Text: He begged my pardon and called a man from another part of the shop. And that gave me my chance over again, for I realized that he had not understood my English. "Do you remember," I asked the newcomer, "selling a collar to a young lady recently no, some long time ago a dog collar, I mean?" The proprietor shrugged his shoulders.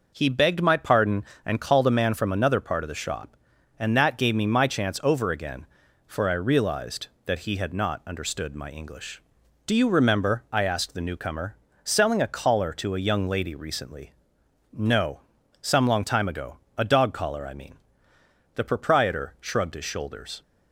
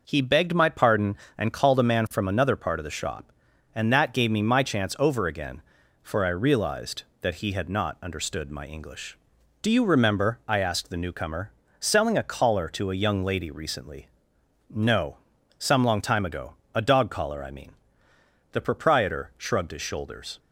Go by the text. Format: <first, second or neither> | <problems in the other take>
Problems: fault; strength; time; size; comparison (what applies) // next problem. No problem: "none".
neither | pauses between "recently" and "no"; noticeable; the same in both // pauses between "ago" and "a"; slight; the same in both